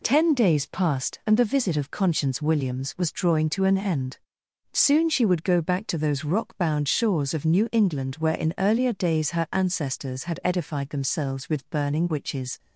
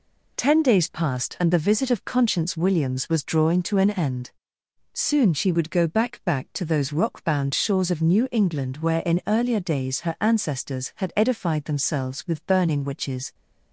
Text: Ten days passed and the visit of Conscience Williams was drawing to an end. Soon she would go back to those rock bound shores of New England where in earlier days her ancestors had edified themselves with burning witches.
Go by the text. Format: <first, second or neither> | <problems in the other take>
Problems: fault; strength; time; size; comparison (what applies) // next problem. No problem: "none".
first | says "back" twice; at 6.2 s